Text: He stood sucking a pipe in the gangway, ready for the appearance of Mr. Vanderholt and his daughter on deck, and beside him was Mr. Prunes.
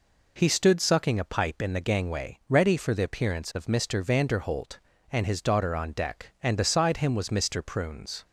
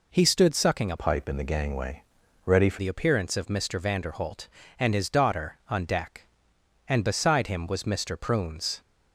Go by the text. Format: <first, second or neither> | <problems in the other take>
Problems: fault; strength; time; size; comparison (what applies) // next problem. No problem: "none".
first | changes voice from "pipe" to "for"; from 0.9 to 2.7 s; 1.8 s long